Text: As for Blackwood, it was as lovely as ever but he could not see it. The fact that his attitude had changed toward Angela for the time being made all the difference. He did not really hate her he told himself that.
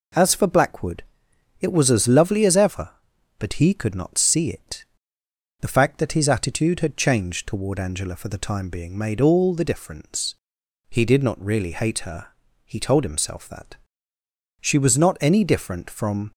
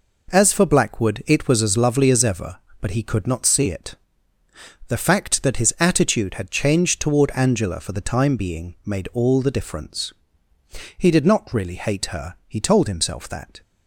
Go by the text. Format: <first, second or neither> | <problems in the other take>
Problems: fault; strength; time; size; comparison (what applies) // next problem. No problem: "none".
second | pauses between "her" and "he"; at 12.2 s; 0.38 s long // goes on to say "She was not any different from"; strong; from 14.6 s on; 1.7 s long